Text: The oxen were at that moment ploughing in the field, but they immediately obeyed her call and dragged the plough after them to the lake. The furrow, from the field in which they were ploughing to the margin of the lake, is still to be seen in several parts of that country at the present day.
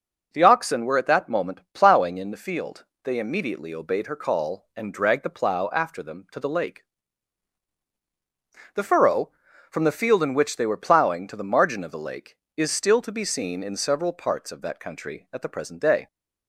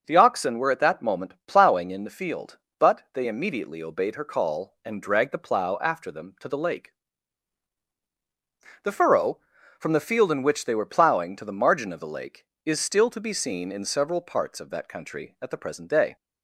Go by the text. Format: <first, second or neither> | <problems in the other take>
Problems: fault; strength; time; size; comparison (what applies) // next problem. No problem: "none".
second | skips "but"; at 2.9 s